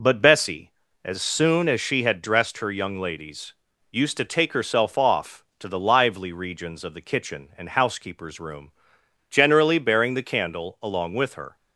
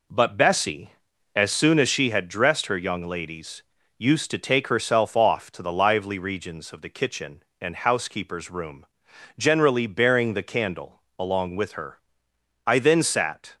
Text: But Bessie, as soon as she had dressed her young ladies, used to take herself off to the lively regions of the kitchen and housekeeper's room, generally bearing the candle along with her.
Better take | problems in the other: first | pauses between "candle" and "along"; slight; at 11.0 s; 0.16 s long // goes on to say "I then sat"; noticeable; from 12.6 s on; 0.90 s long

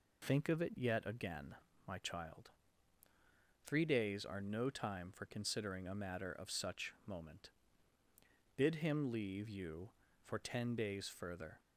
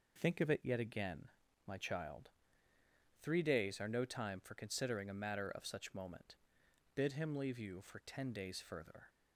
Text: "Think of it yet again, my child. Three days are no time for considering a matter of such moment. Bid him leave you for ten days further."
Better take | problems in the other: neither | none

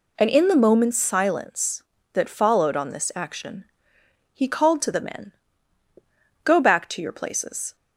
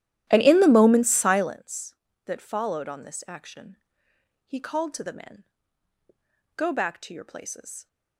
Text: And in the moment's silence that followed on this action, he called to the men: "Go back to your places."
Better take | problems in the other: first | starts louder than the rest; strong; until 1.6 s; 13 dB

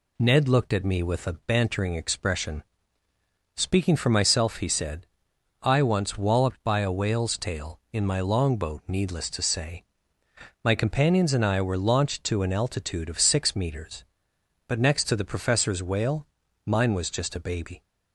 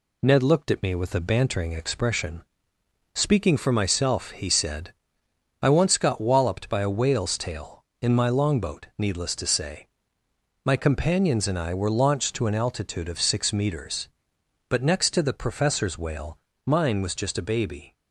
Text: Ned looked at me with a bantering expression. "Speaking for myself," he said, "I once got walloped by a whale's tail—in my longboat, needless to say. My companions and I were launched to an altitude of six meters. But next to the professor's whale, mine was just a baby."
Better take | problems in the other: second | skips "got"; at 6.1 s

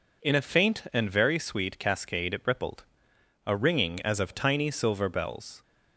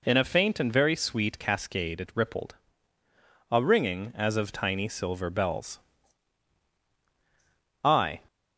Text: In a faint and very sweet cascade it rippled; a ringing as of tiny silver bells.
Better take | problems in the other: first | goes on to say "I"; slight; from 7.8 s on; 0.38 s long

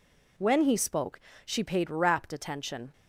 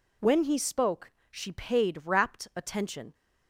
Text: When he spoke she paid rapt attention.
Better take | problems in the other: neither | pauses between "spoke" and "she"; slight; the same in both

